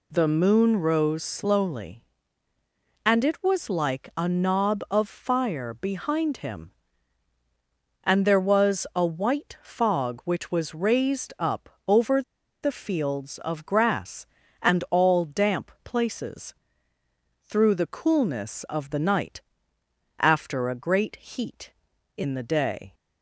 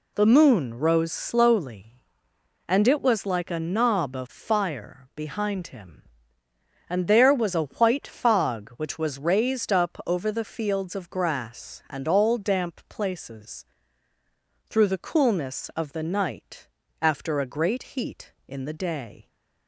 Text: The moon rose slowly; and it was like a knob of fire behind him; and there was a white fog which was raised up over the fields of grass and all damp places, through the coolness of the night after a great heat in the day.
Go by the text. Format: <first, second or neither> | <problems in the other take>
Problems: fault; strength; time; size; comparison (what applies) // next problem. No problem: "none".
second | pauses between "up" and "over"; slight; at 11.6 s; 0.18 s long // pauses between "over" and "the"; at 12.2 s; 0.41 s long // pauses between "night" and "after"; noticeable; at 19.4 s; 0.76 s long; slight in the second